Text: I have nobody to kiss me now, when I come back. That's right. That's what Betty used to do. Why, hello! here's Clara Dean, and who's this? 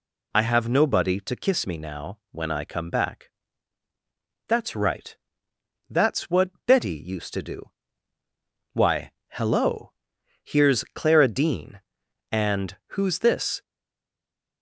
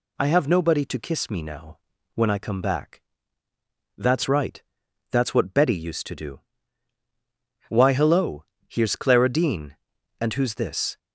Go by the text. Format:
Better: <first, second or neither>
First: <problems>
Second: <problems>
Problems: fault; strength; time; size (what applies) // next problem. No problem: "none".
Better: second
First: pauses between "what" and "Betty"; slight; at 6.5 s; 0.16 s long // pauses between "and" and "who's"; slight; at 12.7 s; 0.16 s long // stays silent after the last word; from 13.6 s on; 1.0 s long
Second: none